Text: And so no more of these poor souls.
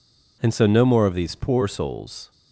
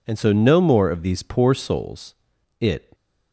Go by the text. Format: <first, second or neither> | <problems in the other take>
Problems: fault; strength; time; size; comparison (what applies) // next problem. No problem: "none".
first | goes on to say "It"; slight; from 2.6 s on; 0.32 s long